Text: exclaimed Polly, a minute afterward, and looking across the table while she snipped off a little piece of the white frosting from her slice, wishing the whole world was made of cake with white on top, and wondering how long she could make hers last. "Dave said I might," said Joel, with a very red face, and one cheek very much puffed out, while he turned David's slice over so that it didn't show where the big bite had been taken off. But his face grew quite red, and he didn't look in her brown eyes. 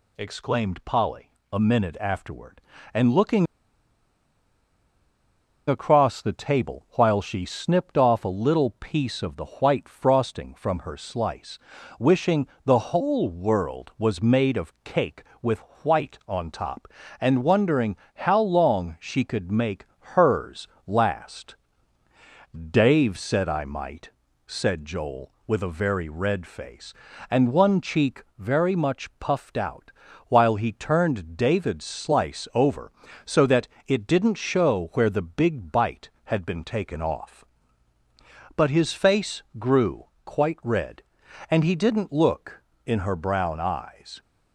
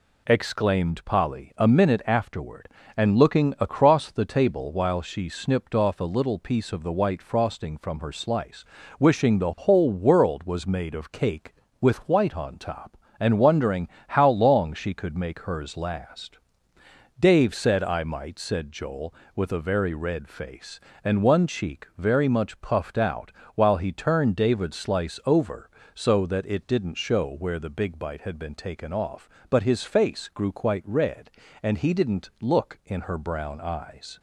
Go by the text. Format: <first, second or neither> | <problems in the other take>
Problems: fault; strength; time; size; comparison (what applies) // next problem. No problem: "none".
second | pauses between "looking" and "across"; strong; at 3.4 s; 2.2 s long // pauses between "wishing" and "the"; slight; at 12.4 s; 0.18 s long // pauses between "with" and "white"; slight; at 15.5 s; 0.24 s long // pauses between "wondering" and "how"; slight; at 17.9 s; 0.20 s long; slight in the second // pauses between "make" and "hers"; slight; at 19.8 s; 0.26 s long // pauses between "hers" and "last"; slight; at 20.6 s; 0.20 s long // pauses between "cheek" and "very"; slight; at 28.2 s; 0.16 s long // pauses between "that" and "it"; slight; at 33.6 s; 0.22 s long // pauses between "grew" and "quite"; slight; at 40.0 s; 0.18 s long